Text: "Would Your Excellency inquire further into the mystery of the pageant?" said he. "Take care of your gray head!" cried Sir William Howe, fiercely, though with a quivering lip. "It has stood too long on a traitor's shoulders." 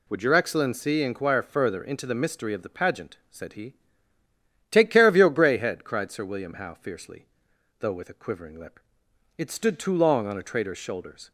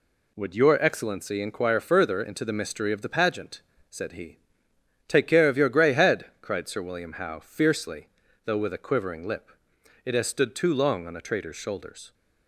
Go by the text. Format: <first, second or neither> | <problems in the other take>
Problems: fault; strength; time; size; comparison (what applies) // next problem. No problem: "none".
second | skips "has"; at 9.5 s